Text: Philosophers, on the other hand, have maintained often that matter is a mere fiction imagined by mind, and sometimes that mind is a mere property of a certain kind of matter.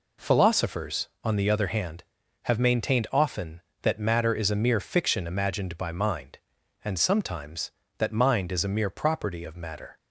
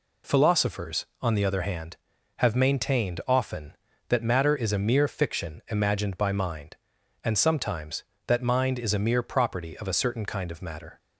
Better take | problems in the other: second | skips "of a certain kind"; at 9.4 s

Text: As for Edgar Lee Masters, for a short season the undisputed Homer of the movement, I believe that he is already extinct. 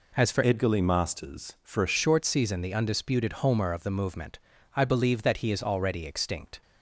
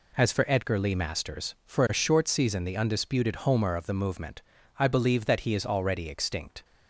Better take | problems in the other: second | changes voice from "Edgar" to "a"; from 0.4 to 1.9 s; 1.5 s long

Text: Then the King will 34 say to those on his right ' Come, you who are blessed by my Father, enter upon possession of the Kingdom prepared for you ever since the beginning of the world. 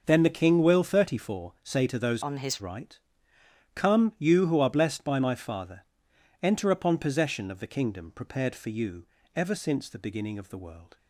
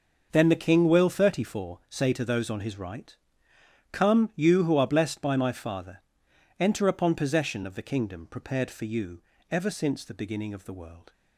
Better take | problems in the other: second | changes voice from "on" to "his"; from 2.2 to 2.6 s; 0.4 s long // pauses between "you" and "ever"; slight; at 9.0 s; 0.32 s long; slight in the second

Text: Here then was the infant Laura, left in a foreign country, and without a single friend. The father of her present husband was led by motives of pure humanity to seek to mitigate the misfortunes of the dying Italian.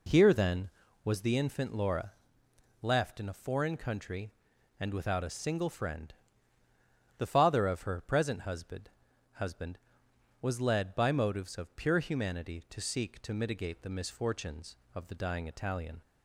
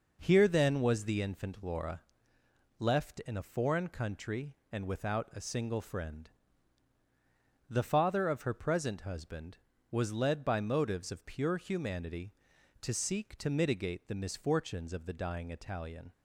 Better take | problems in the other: second | says "husband" twice; at 9.3 s

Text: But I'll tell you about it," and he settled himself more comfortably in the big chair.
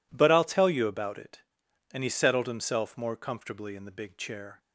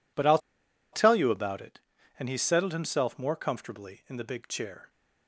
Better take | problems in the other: first | pauses between "I'll" and "tell"; noticeable; at 0.3 s; 0.55 s long

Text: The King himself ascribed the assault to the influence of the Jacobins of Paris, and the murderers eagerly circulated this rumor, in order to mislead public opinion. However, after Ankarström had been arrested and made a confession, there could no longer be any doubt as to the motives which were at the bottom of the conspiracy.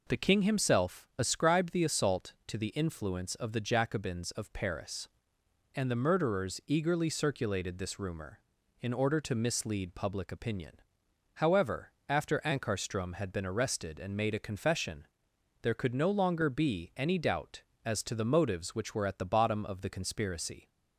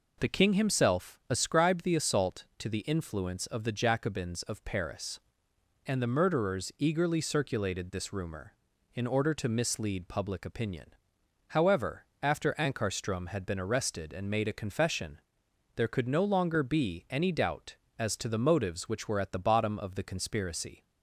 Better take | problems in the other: neither | none

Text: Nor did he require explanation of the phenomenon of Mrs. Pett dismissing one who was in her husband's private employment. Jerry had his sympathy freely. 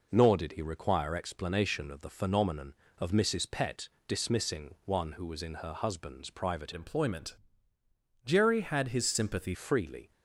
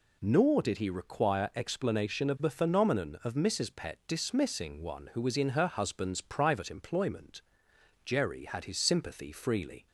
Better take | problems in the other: second | pauses between "Pett" and "dismissing"; slight; at 3.8 s; 0.18 s long // changes voice from "employment" to "sympathy"; from 6.7 to 9.5 s; 2.8 s long

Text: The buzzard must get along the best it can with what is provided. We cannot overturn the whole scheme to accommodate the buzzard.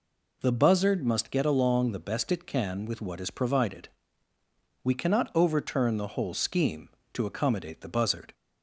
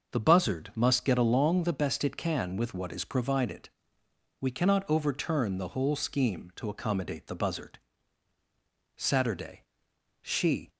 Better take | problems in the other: first | starts louder than the rest; until 1.1 s; 6 dB // goes on to say "Saturday She"; strong; from 8.9 s on; 1.7 s long

